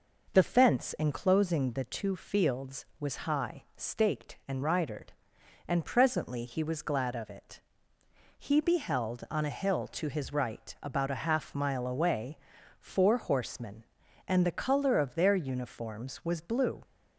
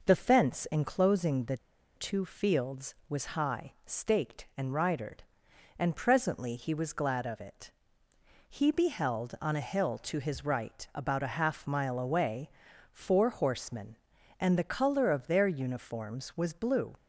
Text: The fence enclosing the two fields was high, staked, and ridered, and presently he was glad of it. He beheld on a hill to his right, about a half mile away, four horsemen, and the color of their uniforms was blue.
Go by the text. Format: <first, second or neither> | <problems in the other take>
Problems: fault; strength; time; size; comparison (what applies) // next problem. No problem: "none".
first | pauses between "the" and "two"; at 1.5 s; 0.38 s long